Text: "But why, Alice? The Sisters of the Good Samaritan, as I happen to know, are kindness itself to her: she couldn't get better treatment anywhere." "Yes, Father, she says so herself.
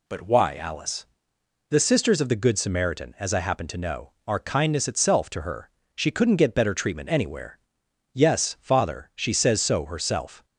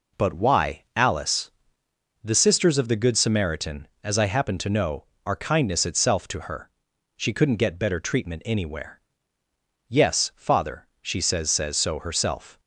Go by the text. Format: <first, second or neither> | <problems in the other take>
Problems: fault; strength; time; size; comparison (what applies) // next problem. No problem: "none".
first | says "says" twice; at 11.4 s